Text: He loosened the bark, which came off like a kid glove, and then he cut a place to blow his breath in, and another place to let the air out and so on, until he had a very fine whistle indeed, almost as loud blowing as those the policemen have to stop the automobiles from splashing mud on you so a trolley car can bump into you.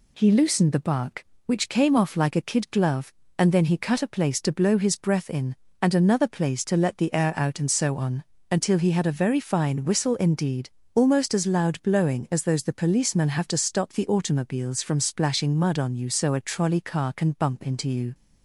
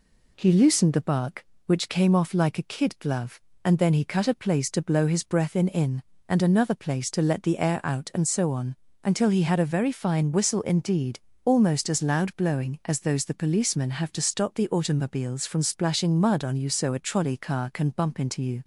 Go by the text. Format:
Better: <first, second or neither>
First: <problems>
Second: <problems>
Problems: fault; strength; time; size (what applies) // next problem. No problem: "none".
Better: first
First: none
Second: says "in" twice; at 5.6 s